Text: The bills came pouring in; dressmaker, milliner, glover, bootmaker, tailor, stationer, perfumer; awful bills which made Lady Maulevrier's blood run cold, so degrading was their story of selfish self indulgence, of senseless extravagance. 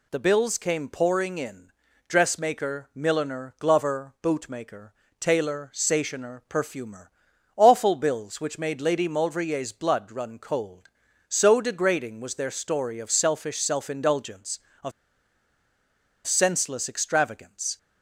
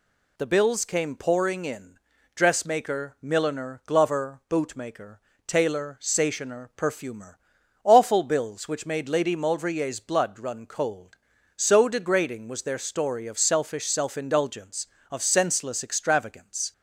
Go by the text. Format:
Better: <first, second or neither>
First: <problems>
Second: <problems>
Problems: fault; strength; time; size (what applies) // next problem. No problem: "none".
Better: second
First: pauses between "of" and "senseless"; strong; at 14.9 s; 1.3 s long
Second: none